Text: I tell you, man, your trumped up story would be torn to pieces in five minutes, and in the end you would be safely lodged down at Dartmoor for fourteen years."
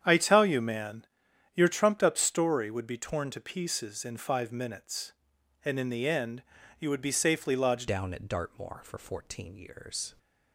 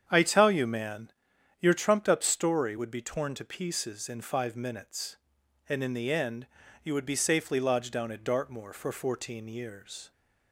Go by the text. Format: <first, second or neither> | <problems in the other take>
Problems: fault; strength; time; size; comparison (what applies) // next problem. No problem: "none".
second | starts louder than the rest; strong; until 1.0 s; 8.5 dB; strong in the second // pauses between "end" and "you"; at 6.4 s; 0.38 s long; also in the second // changes voice at "down"; from 7.8 s on; 2.3 s long